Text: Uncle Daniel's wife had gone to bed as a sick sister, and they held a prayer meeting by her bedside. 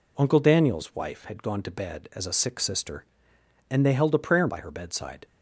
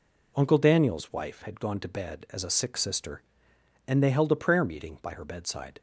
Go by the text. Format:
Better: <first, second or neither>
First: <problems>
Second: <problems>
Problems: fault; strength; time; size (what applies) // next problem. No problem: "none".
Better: second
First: skips "meeting"; at 4.4 s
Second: none